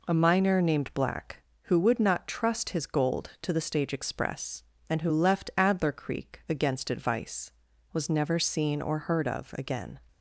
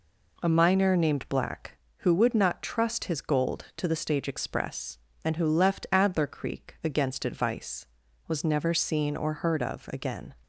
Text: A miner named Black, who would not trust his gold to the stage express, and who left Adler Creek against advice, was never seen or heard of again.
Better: neither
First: none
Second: none

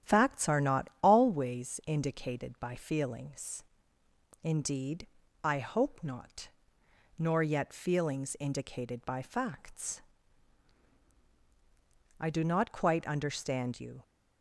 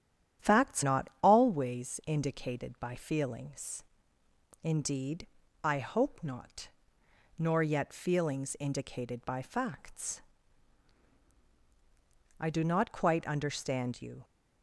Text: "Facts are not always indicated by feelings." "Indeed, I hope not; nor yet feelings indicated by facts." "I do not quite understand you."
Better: first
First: starts louder than the rest; strong; until 1.1 s; 10.5 dB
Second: starts louder than the rest; strong; until 1.5 s; 10.5 dB // skips "are"; at 0.8 s

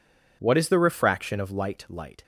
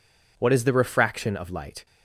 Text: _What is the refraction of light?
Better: second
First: says "light" twice; at 1.8 s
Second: none

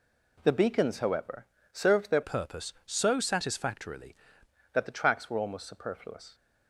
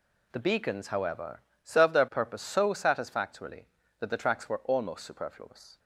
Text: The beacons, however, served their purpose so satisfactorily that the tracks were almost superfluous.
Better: second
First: changes voice from "purpose" to "satisfactorily"; from 2.2 to 4.1 s; 1.9 s long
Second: none

